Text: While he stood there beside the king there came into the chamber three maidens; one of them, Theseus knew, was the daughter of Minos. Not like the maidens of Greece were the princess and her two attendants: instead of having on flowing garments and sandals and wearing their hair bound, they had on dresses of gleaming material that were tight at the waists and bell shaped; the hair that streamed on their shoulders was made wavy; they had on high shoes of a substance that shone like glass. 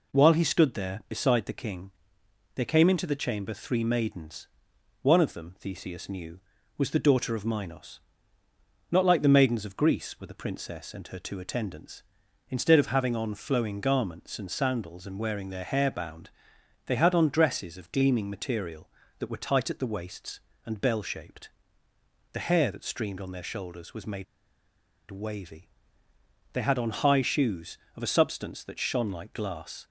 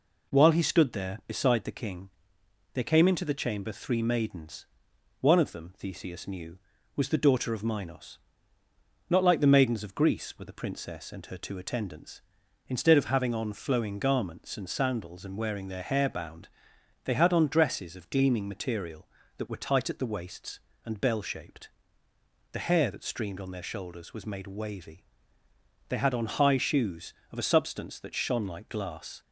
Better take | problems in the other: second | pauses between "king" and "there"; noticeable; at 1.9 s; 0.64 s long; noticeable in the second // pauses between "made" and "wavy"; noticeable; at 24.2 s; 0.86 s long

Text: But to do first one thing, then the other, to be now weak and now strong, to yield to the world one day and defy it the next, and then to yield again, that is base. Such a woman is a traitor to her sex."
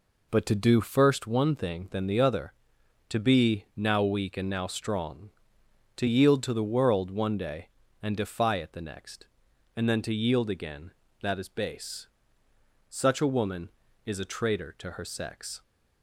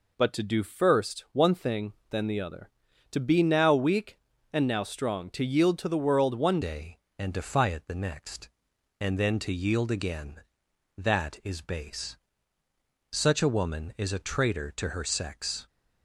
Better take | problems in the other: first | changes voice at "day"; from 6.6 s on; 9.0 s long

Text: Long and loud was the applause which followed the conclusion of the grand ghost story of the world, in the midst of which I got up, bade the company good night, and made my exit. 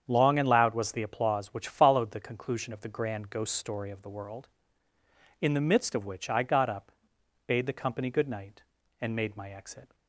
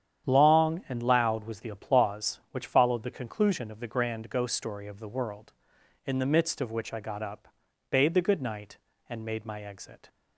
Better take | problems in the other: first | starts louder than the rest; strong; until 1.3 s; 9.5 dB; strong in the first // skips "company"; at 8.2 s

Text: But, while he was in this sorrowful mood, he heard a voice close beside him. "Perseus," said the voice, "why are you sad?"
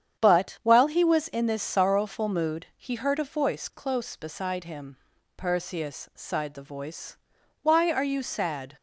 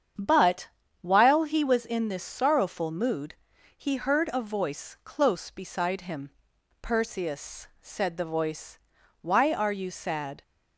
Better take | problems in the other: second | starts louder than the rest; strong; until 1.2 s; 8.5 dB; strong in the second // says "sighed" for "said"; at 6.1 s

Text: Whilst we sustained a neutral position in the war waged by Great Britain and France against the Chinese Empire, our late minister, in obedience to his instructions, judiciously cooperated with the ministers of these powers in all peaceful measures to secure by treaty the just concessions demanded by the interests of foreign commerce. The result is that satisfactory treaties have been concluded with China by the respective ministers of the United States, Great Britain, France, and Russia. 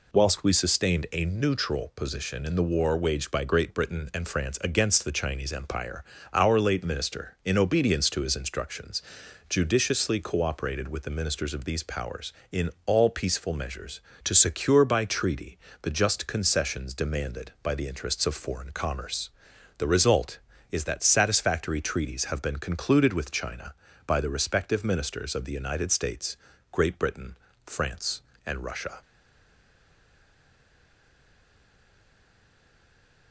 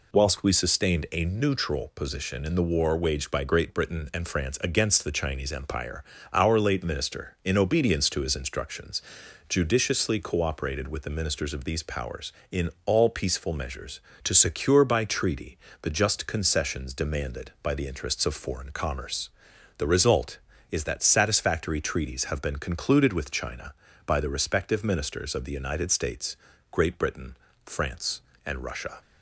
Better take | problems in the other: second | pauses between "treaty" and "the"; slight; at 15.5 s; 0.26 s long; slight in the second // stays silent after the last word; strong; from 29.0 s on; 4.3 s long

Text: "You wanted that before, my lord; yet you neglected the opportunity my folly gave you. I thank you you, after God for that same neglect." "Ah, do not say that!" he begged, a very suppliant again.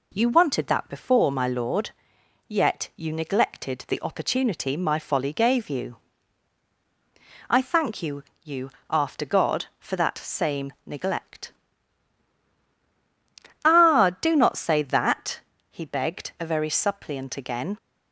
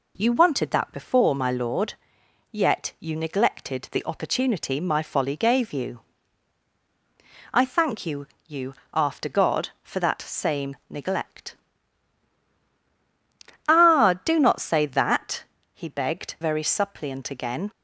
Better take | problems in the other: first | pauses between "you" and "you"; slight; at 8.2 s; 0.22 s long; slight in the first // skips "a"; at 16.3 s

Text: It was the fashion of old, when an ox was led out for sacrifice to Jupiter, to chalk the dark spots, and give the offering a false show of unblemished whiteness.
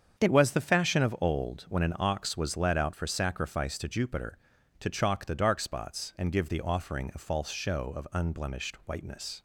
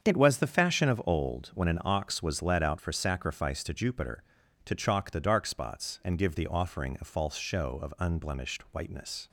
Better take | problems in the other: neither | starts louder than the rest; strong; the same in both

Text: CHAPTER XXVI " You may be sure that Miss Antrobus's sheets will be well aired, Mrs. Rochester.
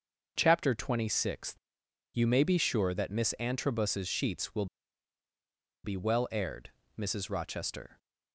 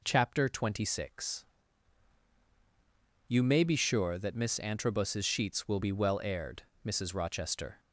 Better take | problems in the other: second | starts louder than the rest; noticeable; until 1.3 s; 6 dB // pauses between "will" and "be"; at 4.6 s; 1.1 s long

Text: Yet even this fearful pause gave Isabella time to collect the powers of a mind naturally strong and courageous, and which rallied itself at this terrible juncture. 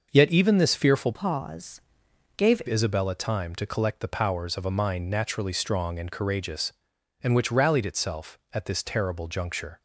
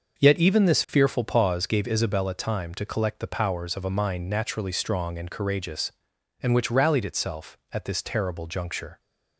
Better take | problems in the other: second | starts louder than the rest; noticeable; until 1.1 s; 6 dB; also in the second // changes voice from "pause" to "gave"; from 1.1 to 2.6 s; 1.5 s long // pauses between "pause" and "gave"; noticeable; at 1.8 s; 0.56 s long

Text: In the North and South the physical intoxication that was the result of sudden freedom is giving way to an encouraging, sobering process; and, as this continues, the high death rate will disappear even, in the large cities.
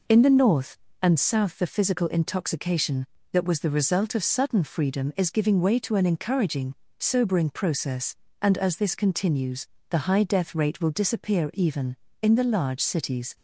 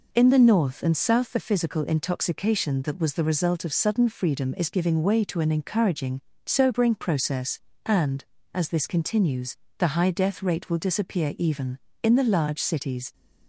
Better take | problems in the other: neither | none

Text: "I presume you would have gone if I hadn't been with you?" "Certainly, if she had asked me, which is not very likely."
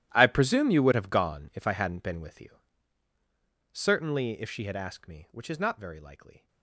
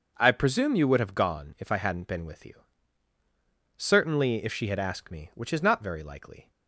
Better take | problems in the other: second | gets quieter; strong; throughout; 17.5 dB // starts louder than the rest; strong; until 1.1 s; 13 dB; noticeable in the second

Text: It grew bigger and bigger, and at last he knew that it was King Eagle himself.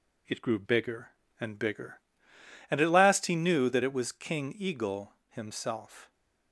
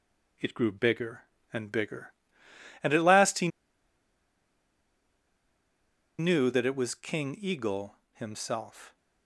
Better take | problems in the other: first | pauses between "he" and "knew"; strong; at 3.4 s; 2.7 s long // pauses between "Eagle" and "himself"; slight; at 7.9 s; 0.20 s long; slight in the first

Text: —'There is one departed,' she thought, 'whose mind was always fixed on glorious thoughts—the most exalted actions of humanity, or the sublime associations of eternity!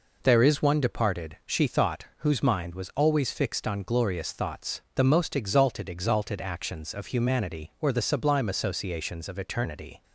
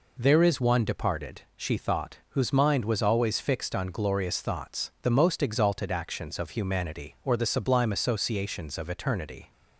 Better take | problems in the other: second | says "exalted" twice; at 5.8 s

